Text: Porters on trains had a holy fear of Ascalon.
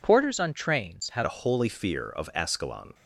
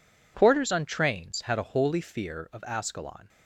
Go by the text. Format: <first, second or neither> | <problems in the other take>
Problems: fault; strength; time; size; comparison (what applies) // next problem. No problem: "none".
second | changes voice at "a"; from 1.2 s on; 1.7 s long